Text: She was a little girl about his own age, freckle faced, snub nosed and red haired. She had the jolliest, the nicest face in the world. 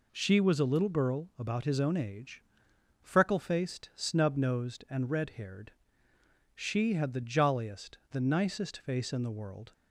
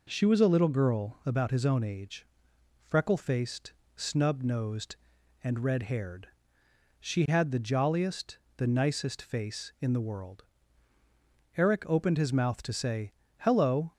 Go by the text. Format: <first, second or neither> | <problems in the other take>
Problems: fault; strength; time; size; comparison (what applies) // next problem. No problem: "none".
first | goes on to say "Eric opened his mouth to say Hello"; strong; from 11.5 s on; 2.3 s long